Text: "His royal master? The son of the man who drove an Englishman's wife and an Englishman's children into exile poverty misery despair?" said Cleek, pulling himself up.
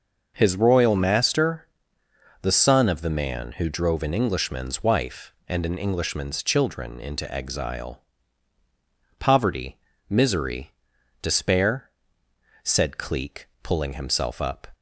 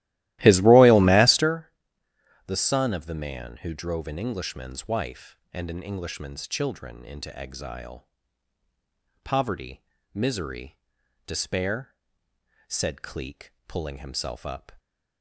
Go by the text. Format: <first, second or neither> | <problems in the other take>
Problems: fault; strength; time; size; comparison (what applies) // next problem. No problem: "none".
first | starts louder than the rest; strong; until 1.6 s; 16 dB // pauses between "exile" and "poverty"; at 8.0 s; 1.1 s long; also in the first // pauses between "poverty" and "misery"; slight; at 9.8 s; 0.32 s long; slight in the first // pauses between "misery" and "despair"; noticeable; at 10.7 s; 0.48 s long; noticeable in the first